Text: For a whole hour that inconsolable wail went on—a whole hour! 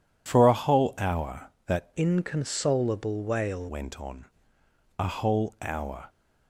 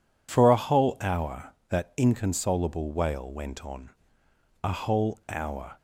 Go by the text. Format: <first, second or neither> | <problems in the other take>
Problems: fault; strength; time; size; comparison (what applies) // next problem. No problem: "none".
second | changes voice from "inconsolable" to "wail"; from 1.9 to 3.6 s; 1.7 s long